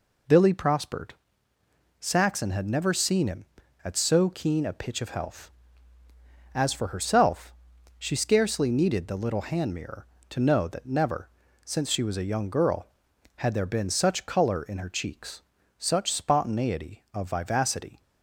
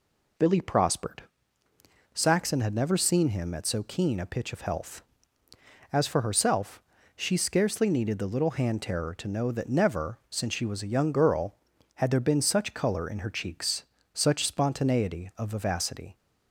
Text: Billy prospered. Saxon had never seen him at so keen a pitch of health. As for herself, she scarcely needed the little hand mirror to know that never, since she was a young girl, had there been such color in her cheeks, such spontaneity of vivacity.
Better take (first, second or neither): first